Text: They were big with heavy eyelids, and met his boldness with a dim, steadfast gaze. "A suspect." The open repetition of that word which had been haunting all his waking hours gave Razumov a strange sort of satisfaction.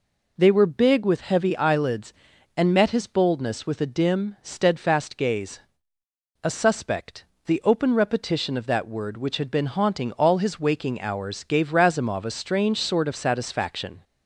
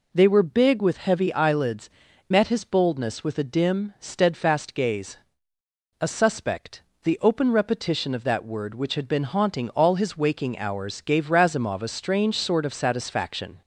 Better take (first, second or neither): first